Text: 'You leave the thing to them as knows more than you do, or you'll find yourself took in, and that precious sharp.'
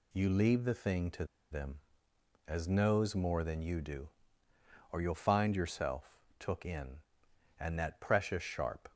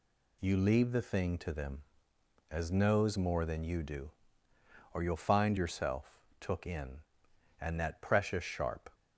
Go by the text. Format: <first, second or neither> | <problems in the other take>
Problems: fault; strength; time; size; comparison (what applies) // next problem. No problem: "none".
second | pauses between "to" and "them"; slight; at 1.2 s; 0.27 s long // pauses between "yourself" and "took"; slight; at 6.1 s; 0.20 s long; slight in the second